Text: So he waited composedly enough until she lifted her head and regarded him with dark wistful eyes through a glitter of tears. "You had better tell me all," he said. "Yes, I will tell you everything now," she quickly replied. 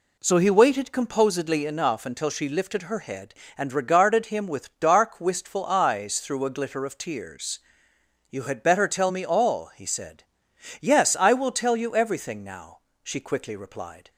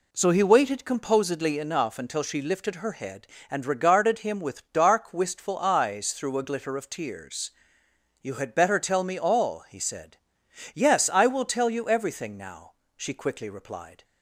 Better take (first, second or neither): neither